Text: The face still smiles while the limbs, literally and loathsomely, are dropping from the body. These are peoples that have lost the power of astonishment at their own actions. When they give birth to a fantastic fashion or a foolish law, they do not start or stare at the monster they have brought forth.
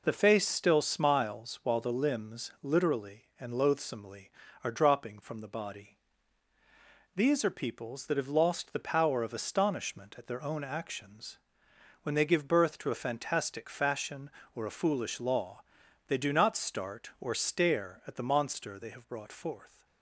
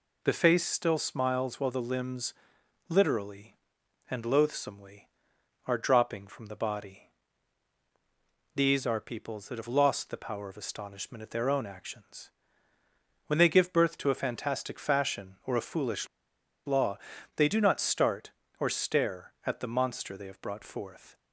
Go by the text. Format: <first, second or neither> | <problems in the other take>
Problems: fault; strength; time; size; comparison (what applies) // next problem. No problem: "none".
first | pauses between "foolish" and "law"; noticeable; at 16.0 s; 0.58 s long